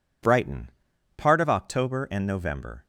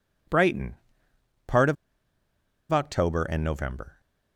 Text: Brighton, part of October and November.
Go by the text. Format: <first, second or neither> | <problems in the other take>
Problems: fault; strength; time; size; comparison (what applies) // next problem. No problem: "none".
first | pauses between "of" and "October"; noticeable; at 1.7 s; 0.96 s long